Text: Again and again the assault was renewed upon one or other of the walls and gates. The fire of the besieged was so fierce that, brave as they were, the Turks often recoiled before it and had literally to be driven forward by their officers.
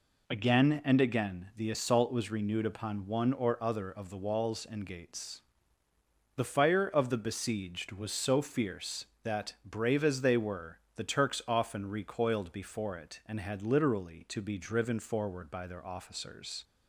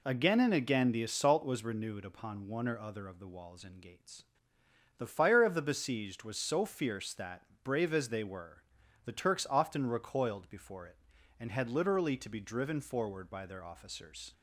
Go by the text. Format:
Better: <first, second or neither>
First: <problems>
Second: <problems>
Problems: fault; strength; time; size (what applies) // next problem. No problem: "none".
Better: neither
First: none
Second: none